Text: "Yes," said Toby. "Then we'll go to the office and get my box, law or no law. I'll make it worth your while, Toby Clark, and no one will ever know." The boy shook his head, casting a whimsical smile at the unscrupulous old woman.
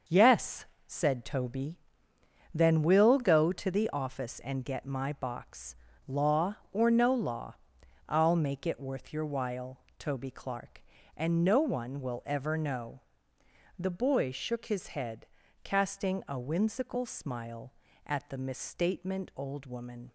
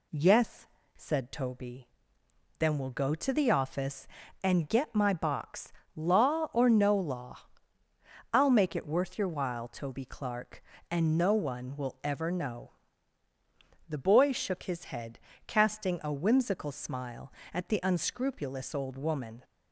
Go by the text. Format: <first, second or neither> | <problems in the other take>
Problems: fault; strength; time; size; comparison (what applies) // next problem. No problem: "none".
second | starts louder than the rest; until 1.2 s; 6.5 dB // says "misstatement" for "unscrupulous"; at 18.3 s